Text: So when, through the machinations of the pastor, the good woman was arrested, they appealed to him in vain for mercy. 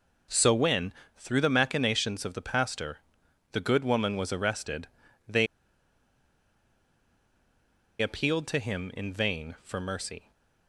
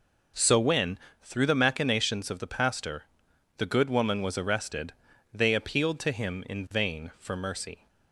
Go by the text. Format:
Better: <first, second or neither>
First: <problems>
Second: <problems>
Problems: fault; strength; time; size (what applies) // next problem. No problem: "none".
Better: second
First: pauses between "they" and "appealed"; strong; at 5.4 s; 2.5 s long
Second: none